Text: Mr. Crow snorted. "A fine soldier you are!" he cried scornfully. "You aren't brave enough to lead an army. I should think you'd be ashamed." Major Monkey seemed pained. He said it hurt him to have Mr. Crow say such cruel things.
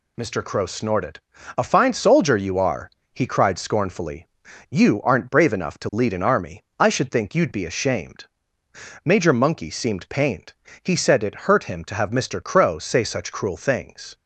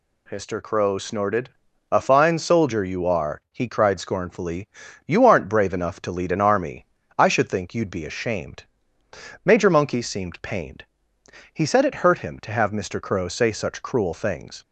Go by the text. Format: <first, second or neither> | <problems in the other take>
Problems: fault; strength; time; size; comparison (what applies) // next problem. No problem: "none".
neither | none